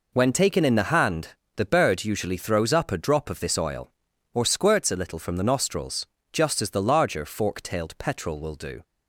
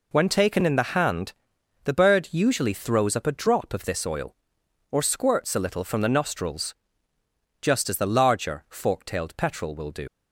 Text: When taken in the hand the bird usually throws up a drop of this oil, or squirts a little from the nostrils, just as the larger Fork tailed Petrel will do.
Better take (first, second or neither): first